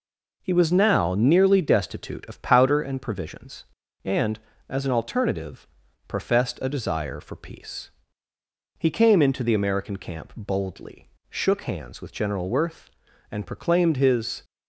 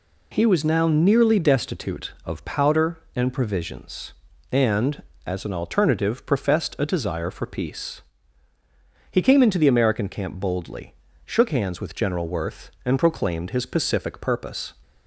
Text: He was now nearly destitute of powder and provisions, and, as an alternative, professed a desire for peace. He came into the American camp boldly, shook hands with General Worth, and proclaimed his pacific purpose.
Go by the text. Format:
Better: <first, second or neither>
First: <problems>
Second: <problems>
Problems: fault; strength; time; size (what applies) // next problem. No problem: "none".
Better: second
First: stops before "pacific purpose"; at 14.4 s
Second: none